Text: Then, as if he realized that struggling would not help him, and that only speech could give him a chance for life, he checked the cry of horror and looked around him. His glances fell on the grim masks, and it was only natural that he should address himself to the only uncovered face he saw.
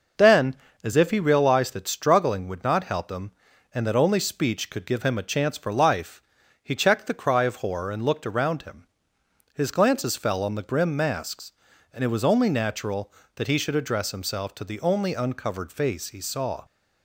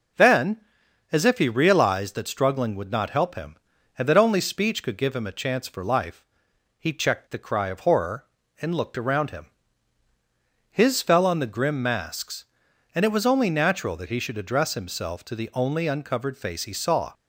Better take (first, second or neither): first